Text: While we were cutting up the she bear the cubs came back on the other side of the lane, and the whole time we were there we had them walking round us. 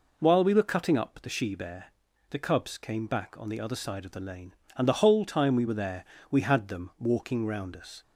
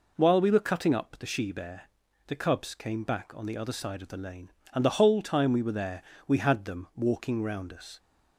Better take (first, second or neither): neither